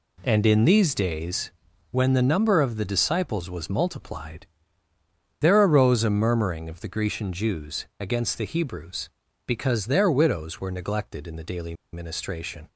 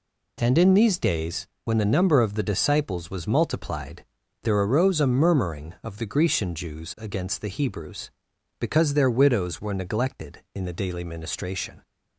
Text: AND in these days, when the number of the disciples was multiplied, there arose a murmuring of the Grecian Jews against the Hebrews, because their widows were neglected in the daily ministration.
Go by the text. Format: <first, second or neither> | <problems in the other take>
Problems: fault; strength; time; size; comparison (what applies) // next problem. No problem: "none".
second | pauses between "daily" and "ministration"; slight; at 11.7 s; 0.20 s long